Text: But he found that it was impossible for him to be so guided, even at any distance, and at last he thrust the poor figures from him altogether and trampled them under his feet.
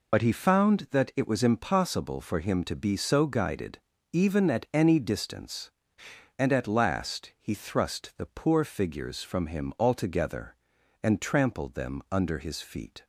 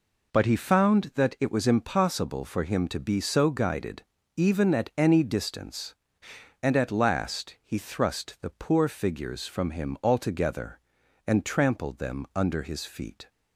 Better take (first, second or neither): second